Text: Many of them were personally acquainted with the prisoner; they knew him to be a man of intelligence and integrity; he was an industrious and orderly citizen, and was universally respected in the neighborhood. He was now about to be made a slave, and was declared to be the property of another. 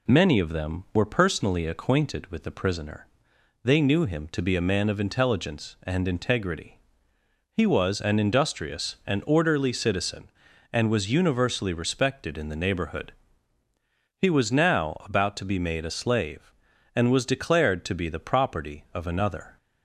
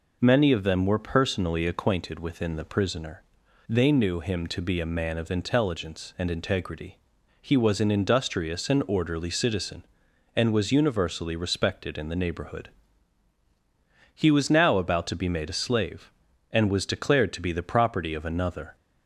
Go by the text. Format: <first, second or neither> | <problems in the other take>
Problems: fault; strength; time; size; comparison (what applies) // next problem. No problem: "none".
first | says "within" for "with"; at 2.1 s